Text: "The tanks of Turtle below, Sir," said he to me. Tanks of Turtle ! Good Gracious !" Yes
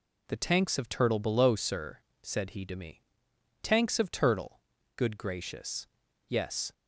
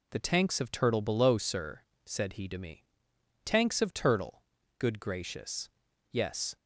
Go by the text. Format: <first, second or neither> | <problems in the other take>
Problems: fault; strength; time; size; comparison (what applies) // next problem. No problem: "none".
neither | none